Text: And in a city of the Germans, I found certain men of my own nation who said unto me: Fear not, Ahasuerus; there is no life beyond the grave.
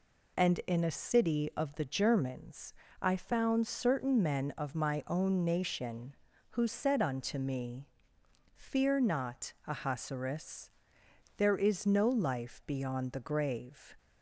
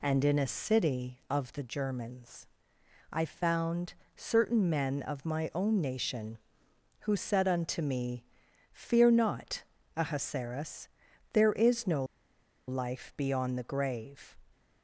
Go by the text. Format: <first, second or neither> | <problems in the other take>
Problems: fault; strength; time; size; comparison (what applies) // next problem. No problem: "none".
first | pauses between "found" and "certain"; slight; at 3.9 s; 0.22 s long // pauses between "no" and "life"; noticeable; at 12.0 s; 0.64 s long